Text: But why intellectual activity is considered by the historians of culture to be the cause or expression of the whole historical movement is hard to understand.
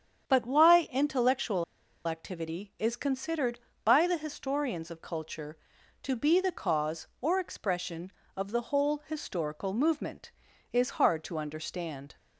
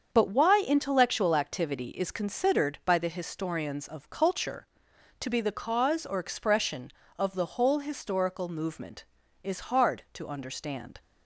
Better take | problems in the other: second | starts louder than the rest; strong; until 1.3 s; 8 dB; also in the second // pauses between "intellectual" and "activity"; at 1.6 s; 0.44 s long

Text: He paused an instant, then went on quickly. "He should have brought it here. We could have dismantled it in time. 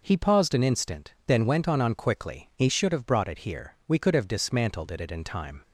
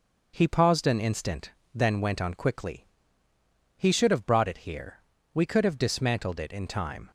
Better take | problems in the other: second | says "on" twice; at 1.7 s

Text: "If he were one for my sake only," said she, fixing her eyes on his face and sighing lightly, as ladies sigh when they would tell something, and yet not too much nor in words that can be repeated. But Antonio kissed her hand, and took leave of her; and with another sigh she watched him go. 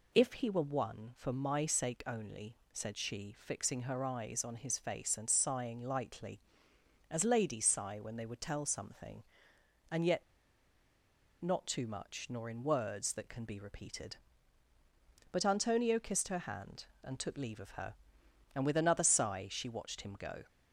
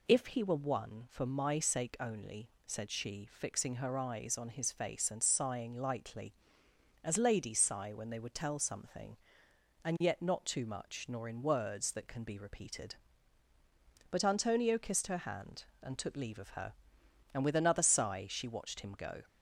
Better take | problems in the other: second | pauses between "yet" and "not"; at 10.2 s; 1.1 s long

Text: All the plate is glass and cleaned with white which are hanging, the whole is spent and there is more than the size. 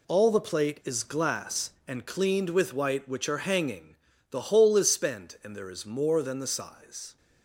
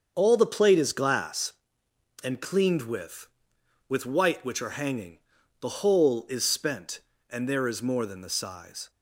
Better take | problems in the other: first | starts louder than the rest; until 1.1 s; 7 dB // says "with" twice; at 3.8 s

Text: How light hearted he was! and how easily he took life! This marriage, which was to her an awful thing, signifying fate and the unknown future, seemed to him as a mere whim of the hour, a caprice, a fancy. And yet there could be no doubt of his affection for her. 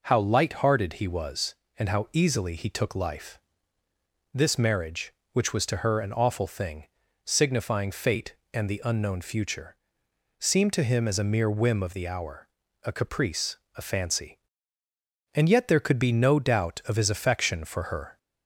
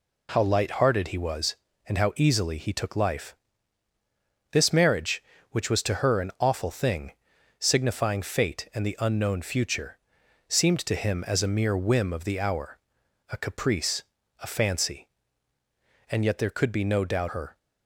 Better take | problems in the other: first | skips "of his affection for"; at 17.2 s

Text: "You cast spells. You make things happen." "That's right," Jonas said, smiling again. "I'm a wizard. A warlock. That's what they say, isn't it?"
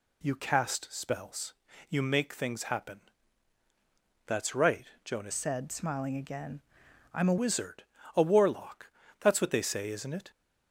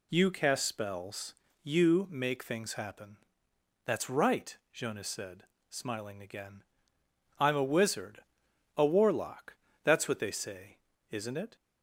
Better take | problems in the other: second | changes voice from "said" to "a"; from 5.3 to 7.3 s; 2.0 s long

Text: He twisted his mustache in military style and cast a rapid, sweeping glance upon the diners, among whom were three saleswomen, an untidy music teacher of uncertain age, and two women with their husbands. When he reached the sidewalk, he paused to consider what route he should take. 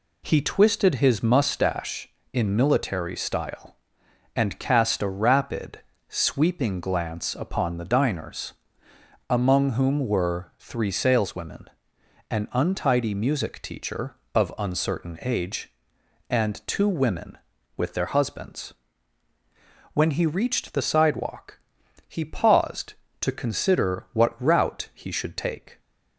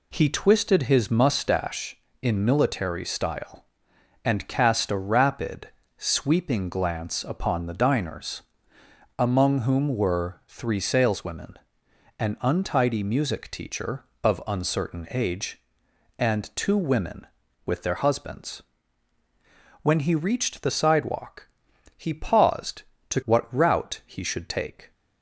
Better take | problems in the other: first | skips "consider"; at 23.2 s

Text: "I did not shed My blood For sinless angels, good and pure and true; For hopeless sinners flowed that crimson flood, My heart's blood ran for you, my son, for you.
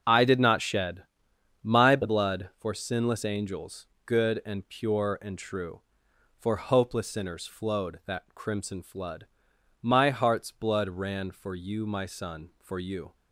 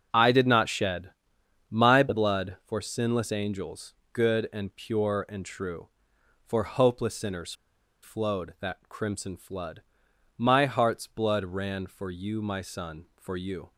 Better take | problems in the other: first | starts louder than the rest; until 1.7 s; 6.5 dB; also in the first // pauses between "shed" and "My"; noticeable; at 1.1 s; 0.58 s long; noticeable in the first // pauses between "sinners" and "flowed"; noticeable; at 7.5 s; 0.50 s long

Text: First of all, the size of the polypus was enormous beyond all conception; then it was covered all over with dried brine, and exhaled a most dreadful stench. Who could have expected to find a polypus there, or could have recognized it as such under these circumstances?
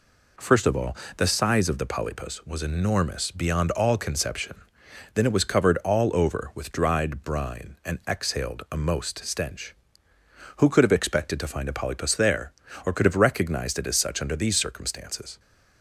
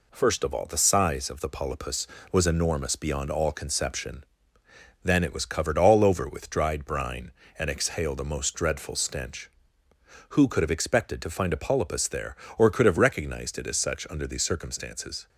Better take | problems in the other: second | skips "dreadful"; at 9.2 s

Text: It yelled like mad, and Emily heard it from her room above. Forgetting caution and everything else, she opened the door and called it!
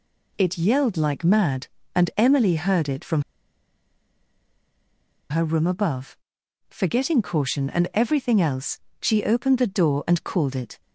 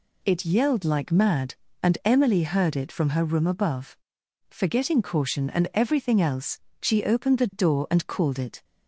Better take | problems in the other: second | pauses between "from" and "her"; strong; at 3.2 s; 2.0 s long

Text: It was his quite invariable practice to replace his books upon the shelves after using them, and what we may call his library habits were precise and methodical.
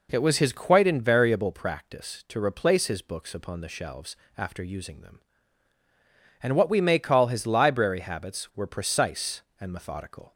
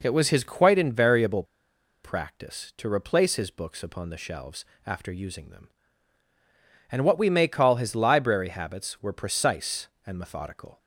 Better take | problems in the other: first | pauses between "invariable" and "practice"; noticeable; at 1.4 s; 0.60 s long // pauses between "shelves" and "after"; slight; at 4.6 s; 0.20 s long; slight in the first

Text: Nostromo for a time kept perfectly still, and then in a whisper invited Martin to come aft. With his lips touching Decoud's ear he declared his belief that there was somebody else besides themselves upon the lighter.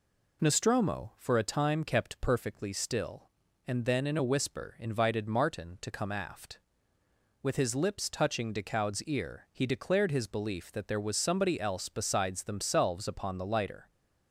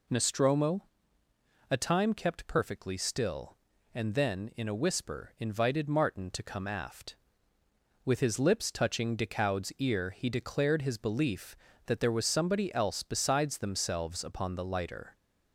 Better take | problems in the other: first | skips "for"; at 1.2 s

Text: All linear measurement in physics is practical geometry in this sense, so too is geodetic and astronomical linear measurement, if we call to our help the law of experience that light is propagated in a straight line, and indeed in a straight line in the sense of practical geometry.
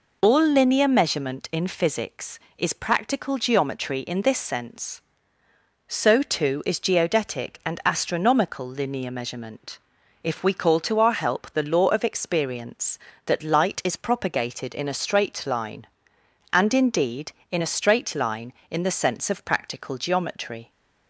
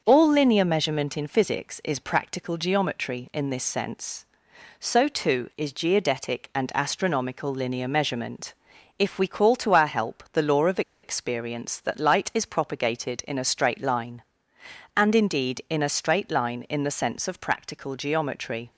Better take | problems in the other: first | starts louder than the rest; until 1.0 s; 6.5 dB // pauses between "of" and "experience"; slight; at 10.8 s; 0.22 s long

